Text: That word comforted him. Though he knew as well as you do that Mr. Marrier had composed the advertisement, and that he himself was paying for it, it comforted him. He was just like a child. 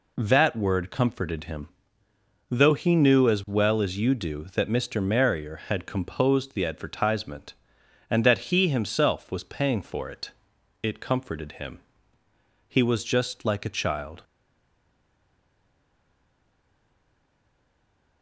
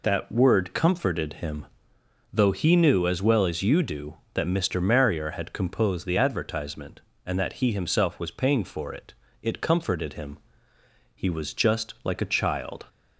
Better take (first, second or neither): second